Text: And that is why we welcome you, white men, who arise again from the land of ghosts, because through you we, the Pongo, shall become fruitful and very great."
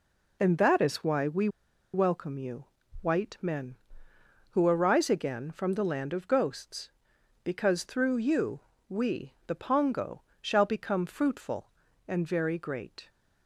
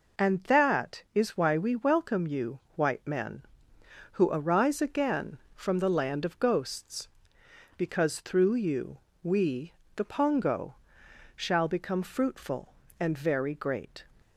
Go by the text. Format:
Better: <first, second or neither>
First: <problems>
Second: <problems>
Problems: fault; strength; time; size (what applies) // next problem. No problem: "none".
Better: second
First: pauses between "we" and "welcome"; at 1.4 s; 0.45 s long // pauses between "you" and "we"; slight; at 8.6 s; 0.28 s long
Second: pauses between "you" and "we"; slight; at 8.9 s; 0.26 s long